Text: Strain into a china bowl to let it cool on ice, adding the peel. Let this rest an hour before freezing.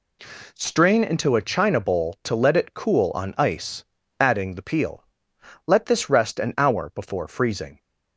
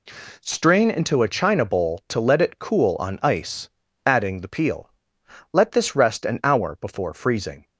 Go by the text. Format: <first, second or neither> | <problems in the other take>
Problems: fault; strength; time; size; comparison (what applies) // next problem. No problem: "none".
neither | none